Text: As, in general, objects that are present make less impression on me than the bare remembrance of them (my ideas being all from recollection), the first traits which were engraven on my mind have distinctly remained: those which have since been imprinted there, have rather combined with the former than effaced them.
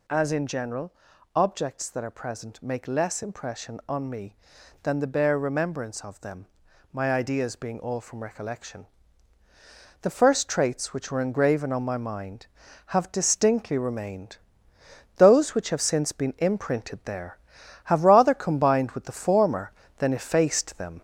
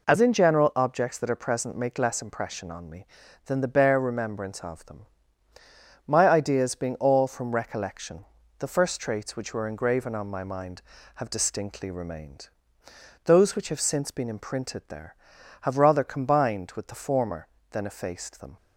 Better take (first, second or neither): second